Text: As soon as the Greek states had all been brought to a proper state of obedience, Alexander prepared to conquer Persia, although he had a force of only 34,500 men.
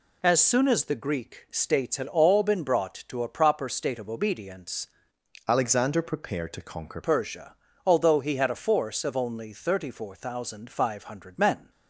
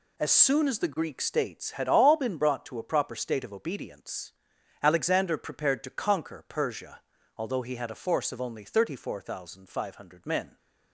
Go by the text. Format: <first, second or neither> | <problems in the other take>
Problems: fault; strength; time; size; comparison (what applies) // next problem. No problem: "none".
second | changes voice from "Alexander" to "conquer"; from 5.4 to 7.0 s; 1.6 s long